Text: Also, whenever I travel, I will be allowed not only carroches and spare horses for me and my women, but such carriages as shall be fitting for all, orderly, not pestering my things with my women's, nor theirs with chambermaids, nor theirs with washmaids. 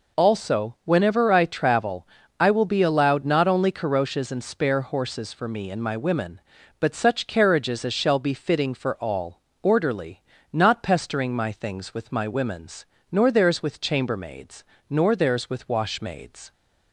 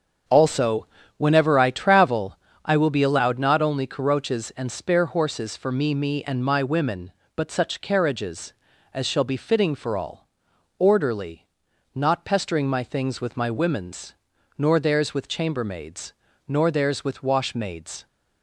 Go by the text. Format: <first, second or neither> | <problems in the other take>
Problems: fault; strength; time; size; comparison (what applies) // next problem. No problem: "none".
first | starts louder than the rest; until 1.5 s; 7 dB // says "me" twice; at 5.9 s